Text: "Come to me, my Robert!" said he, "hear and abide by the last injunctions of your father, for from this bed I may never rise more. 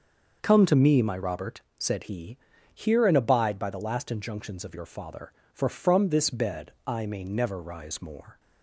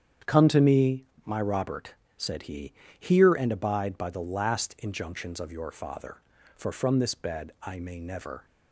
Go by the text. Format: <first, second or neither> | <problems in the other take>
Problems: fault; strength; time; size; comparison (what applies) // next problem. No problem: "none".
first | starts louder than the rest; strong; until 1.4 s; 8.5 dB; also in the first // stops before "rise more"; at 8.4 s